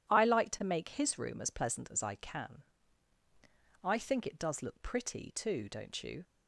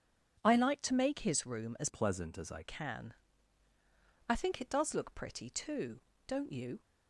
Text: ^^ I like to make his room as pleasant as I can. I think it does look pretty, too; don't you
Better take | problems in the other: first | changes voice from "pleasant" to "I"; from 1.8 to 2.6 s; 0.8 s long

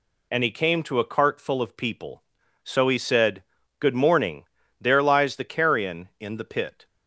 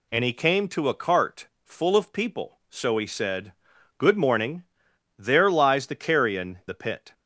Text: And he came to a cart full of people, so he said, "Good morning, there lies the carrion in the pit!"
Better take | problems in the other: first | pauses between "cart" and "full"; slight; at 1.4 s; 0.16 s long // skips "in"; at 6.6 s

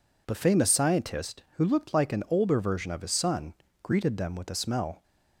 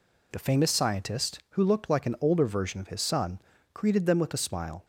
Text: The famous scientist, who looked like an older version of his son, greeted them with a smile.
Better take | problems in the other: second | says "smell" for "smile"; at 4.5 s

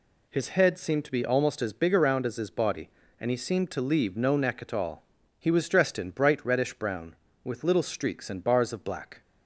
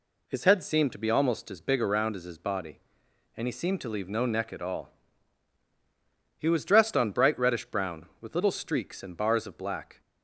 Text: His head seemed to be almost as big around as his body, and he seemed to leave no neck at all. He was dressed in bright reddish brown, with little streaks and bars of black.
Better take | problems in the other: first | says "on" for "in"; at 6.9 s

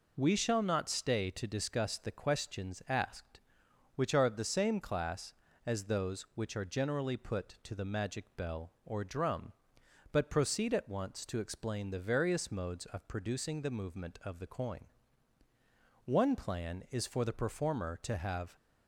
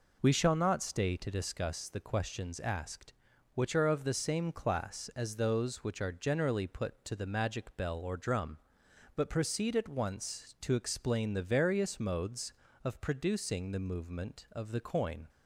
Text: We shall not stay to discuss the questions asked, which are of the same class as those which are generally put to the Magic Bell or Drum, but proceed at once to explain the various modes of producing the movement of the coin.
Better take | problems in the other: second | goes on to say "One plan is for the performer to have"; strong; from 16.0 s on; 2.5 s long

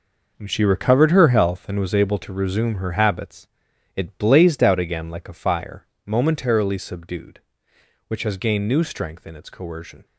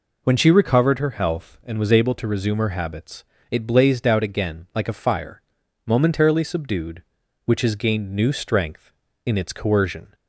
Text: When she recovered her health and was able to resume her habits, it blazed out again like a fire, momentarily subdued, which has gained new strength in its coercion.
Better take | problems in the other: second | gets quieter; strong; throughout; 9.5 dB

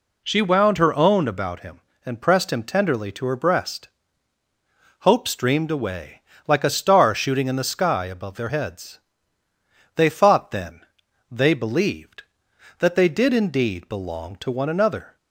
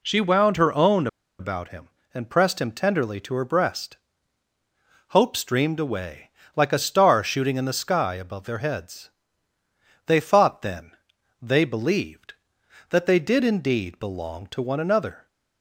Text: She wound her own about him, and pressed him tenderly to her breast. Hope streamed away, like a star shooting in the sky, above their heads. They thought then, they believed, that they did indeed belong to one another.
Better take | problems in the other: first | pauses between "own" and "about"; slight; at 1.0 s; 0.32 s long

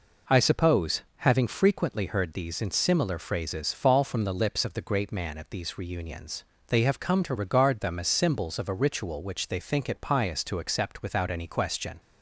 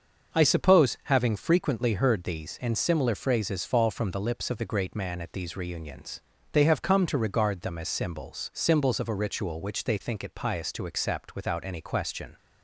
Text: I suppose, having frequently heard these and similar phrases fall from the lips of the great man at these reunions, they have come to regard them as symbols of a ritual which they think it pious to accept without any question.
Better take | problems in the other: first | starts louder than the rest; until 1.4 s; 6.5 dB // says "symbols" twice; at 8.5 s

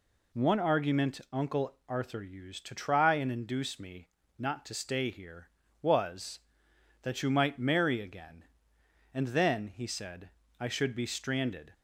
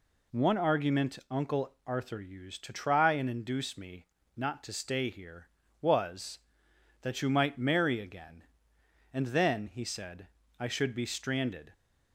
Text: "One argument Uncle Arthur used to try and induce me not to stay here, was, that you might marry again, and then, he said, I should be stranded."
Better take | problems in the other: neither | pauses between "me" and "not"; slight; the same in both

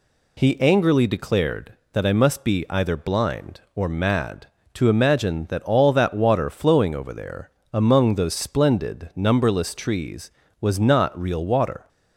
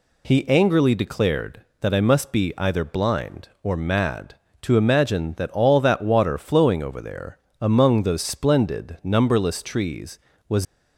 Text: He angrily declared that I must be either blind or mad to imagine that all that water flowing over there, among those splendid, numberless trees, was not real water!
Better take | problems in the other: first | stops before "not real water"; at 10.6 s

